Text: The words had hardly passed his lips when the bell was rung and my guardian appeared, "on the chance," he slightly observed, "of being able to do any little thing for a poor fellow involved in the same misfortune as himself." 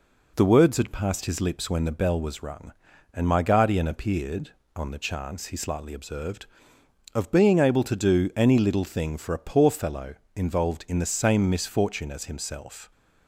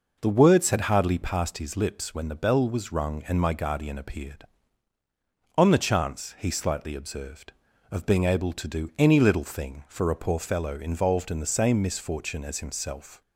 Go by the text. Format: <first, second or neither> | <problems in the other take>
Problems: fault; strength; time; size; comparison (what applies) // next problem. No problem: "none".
second | skips "hardly"; at 0.9 s // pauses between "fellow" and "involved"; slight; at 10.1 s; 0.20 s long